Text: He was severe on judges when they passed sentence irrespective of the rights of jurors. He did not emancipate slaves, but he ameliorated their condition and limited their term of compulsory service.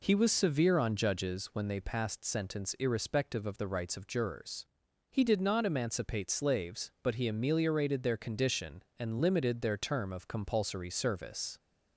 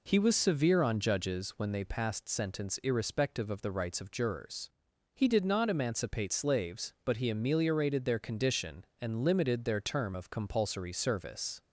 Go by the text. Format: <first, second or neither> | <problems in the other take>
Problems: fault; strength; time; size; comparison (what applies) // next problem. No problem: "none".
neither | none